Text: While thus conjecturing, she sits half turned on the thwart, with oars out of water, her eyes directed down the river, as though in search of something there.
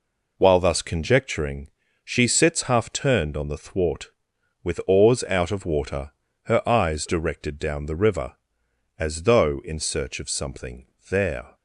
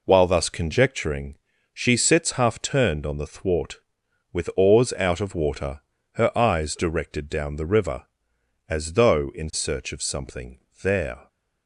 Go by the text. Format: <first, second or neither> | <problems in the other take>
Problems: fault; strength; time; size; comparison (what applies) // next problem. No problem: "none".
neither | pauses between "something" and "there"; slight; the same in both